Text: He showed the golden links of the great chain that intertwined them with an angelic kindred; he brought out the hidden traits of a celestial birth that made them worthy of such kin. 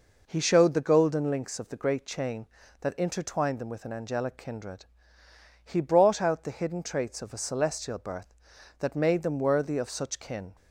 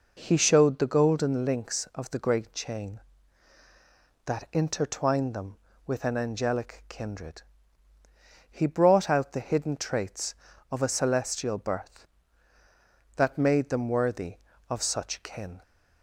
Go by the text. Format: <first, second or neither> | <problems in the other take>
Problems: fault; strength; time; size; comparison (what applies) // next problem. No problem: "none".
neither | none